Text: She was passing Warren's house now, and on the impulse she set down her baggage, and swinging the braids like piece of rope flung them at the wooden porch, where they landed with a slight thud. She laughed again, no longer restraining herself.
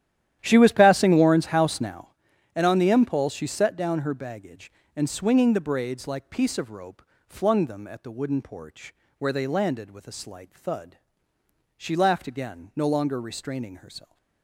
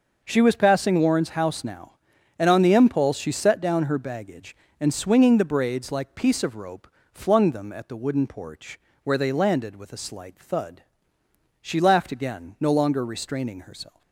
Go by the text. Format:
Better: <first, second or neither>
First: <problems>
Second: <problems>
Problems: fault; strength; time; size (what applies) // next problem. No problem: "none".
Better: second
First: starts louder than the rest; strong; until 2.2 s; 11.5 dB // pauses between "rope" and "flung"; slight; at 7.0 s; 0.24 s long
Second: pauses between "rope" and "flung"; slight; at 6.8 s; 0.24 s long